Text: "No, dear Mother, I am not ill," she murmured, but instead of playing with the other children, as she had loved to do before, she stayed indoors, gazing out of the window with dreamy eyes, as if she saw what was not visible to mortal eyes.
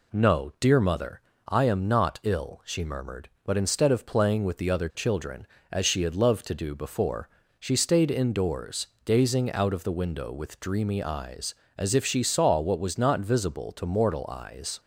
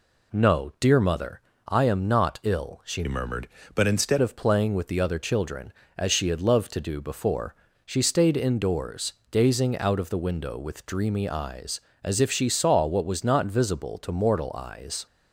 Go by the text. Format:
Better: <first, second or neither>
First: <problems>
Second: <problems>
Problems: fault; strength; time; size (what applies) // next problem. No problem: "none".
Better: first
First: none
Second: changes voice from "murmured" to "instead"; from 3.0 to 4.1 s; 1.1 s long